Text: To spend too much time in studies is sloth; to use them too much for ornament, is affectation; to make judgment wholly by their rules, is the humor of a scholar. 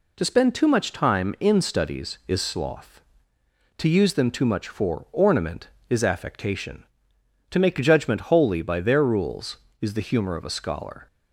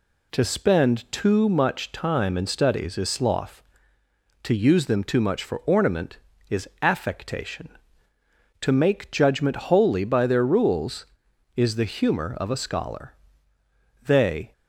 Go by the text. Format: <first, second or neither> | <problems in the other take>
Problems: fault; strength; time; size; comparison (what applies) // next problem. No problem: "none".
first | pauses between "is" and "affectation"; slight; at 6.6 s; 0.16 s long // goes on to say "They"; slight; from 14.0 s on; 0.46 s long